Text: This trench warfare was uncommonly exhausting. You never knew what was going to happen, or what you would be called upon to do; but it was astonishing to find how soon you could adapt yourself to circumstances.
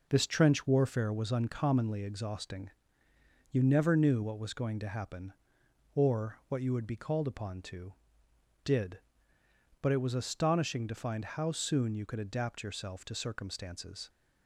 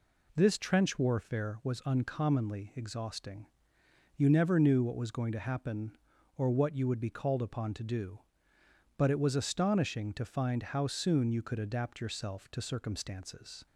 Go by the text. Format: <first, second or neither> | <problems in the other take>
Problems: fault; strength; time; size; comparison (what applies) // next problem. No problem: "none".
second | says "did" for "do"; at 8.6 s